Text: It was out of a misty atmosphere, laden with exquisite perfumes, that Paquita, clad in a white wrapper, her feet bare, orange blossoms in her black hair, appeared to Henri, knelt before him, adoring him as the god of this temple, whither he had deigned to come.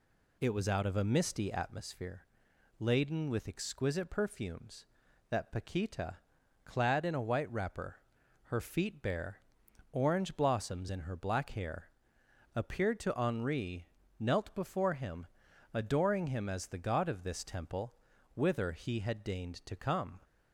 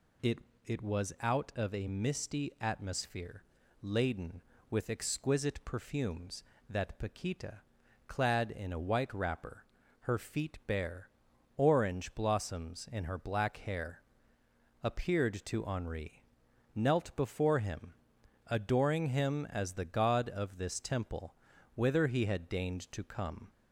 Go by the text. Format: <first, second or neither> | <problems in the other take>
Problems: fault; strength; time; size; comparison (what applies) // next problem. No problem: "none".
first | says "It" twice; at 0.6 s